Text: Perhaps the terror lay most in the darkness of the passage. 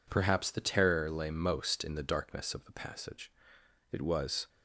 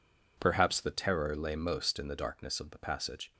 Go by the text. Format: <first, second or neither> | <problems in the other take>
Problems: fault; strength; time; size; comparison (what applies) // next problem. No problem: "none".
second | goes on to say "It was"; from 3.9 s on; 0.56 s long